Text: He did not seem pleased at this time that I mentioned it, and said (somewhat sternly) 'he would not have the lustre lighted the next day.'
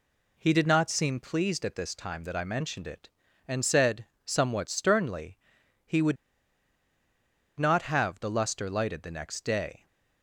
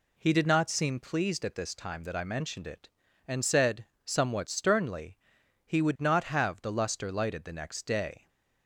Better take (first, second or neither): second